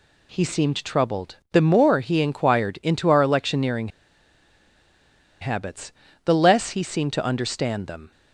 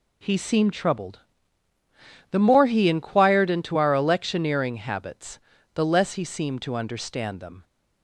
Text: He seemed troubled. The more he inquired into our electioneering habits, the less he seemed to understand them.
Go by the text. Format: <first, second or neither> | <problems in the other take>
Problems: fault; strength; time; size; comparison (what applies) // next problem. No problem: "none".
second | pauses between "electioneering" and "habits"; strong; at 3.8 s; 1.5 s long